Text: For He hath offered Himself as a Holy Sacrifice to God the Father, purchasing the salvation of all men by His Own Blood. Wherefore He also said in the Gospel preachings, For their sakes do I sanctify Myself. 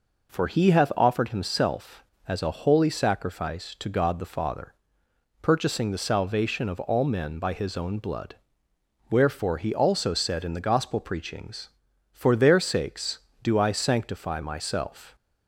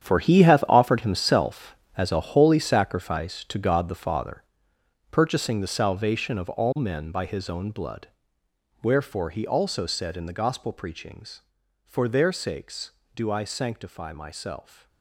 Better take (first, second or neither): first